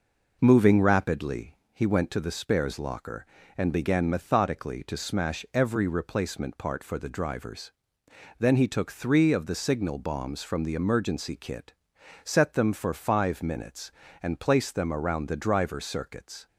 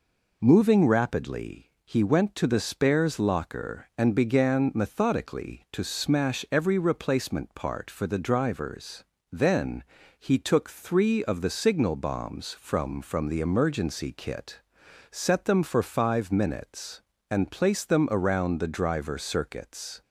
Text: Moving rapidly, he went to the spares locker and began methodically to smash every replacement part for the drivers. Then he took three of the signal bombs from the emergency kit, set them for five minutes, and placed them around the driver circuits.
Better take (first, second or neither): first